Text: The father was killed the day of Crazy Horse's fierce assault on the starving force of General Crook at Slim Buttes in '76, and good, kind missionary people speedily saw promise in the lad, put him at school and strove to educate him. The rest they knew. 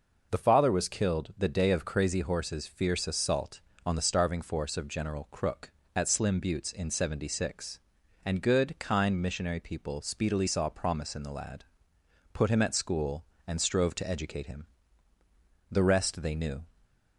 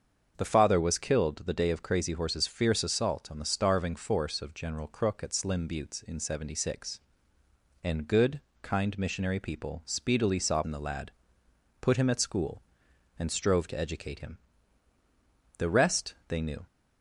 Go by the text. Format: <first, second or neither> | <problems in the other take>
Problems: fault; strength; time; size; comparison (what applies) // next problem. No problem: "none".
first | starts louder than the rest; until 1.3 s; 7 dB // skips "promise"; at 10.6 s